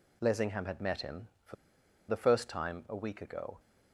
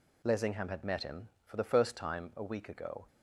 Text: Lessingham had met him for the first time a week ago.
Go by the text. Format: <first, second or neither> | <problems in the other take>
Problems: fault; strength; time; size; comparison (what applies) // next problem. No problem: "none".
second | pauses between "for" and "the"; noticeable; at 1.5 s; 0.55 s long